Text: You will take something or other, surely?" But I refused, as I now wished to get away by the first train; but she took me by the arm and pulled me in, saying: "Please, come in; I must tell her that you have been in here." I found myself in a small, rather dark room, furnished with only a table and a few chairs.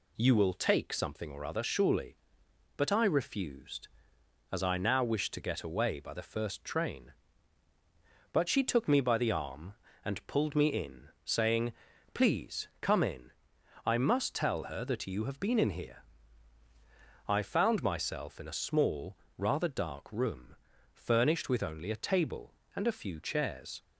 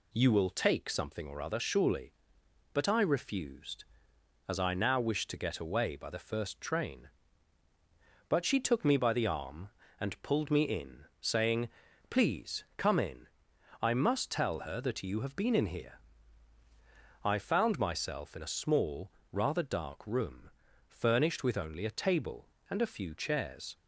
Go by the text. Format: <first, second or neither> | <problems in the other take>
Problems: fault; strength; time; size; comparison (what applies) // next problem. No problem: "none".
neither | none